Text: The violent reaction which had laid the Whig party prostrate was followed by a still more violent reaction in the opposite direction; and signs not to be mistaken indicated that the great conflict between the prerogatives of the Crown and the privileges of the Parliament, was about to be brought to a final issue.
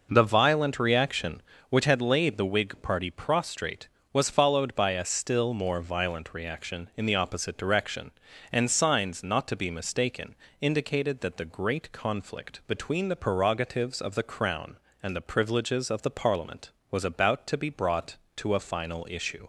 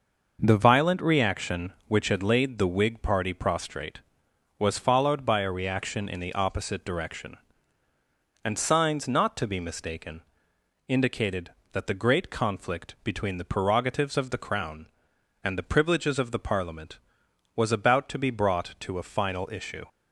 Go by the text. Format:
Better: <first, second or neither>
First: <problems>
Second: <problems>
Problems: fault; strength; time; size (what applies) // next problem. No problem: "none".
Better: first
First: pauses between "mistaken" and "indicated"; slight; at 10.3 s; 0.26 s long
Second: skips "still more violent"; at 5.5 s // pauses between "mistaken" and "indicated"; noticeable; at 10.2 s; 0.66 s long